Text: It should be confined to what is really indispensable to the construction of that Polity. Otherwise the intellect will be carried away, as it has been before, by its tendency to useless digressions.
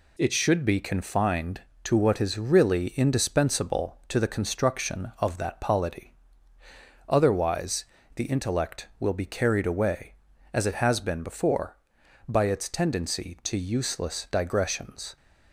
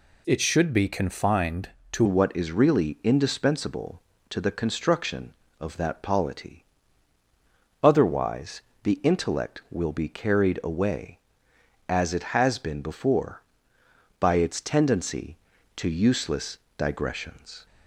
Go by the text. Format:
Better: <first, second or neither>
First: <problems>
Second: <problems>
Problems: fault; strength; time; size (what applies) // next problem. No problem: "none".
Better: first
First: pauses between "Otherwise" and "the"; slight; at 7.8 s; 0.30 s long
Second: changes voice at "what"; from 2.0 s on; 15.6 s long // pauses between "Otherwise" and "the"; slight; at 8.6 s; 0.22 s long // pauses between "useless" and "digressions"; slight; at 16.5 s; 0.20 s long